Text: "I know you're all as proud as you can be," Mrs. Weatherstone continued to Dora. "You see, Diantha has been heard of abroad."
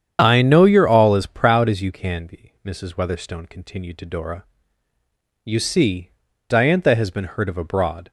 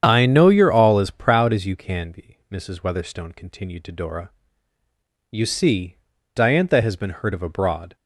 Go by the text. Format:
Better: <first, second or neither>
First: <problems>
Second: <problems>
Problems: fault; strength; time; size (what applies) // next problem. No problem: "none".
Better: neither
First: starts louder than the rest; strong; until 1.2 s; 8.5 dB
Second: starts louder than the rest; strong; until 1.0 s; 8.5 dB